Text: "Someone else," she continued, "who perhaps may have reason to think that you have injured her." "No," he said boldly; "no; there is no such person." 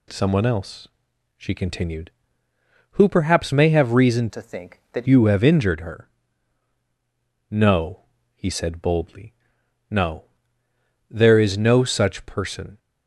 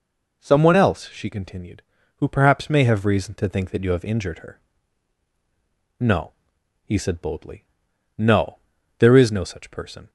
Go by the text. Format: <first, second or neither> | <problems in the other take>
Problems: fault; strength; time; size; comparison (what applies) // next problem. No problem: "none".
second | changes voice from "to" to "that"; from 4.2 to 5.0 s; 0.8 s long